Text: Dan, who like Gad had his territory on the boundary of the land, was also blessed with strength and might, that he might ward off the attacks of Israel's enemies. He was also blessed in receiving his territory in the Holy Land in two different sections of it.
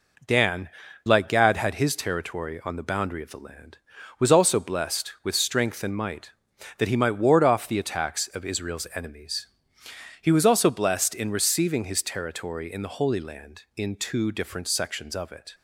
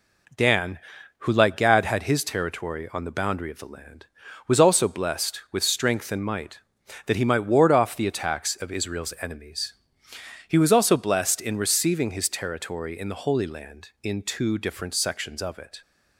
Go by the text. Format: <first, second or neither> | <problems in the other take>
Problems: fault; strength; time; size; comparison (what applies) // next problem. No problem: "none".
second | skips "who"; at 0.8 s